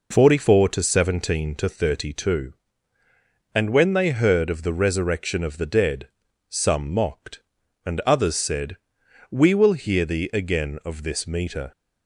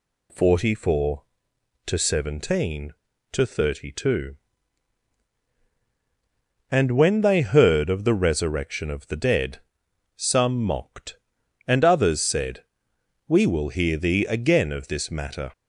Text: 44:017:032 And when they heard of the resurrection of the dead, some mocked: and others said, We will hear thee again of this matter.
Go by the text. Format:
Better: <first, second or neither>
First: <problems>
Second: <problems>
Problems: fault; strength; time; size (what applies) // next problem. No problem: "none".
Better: second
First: says "meter" for "matter"; at 11.2 s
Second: none